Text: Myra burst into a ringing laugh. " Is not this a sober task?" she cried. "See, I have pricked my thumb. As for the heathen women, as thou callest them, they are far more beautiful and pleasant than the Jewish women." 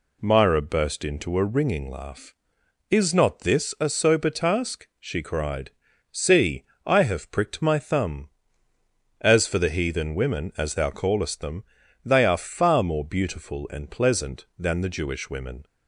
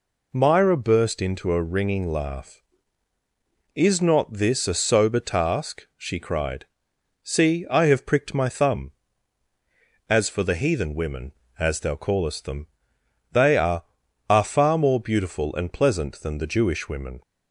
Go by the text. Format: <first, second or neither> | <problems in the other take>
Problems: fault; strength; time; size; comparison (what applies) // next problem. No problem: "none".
first | says "are" twice; at 14.2 s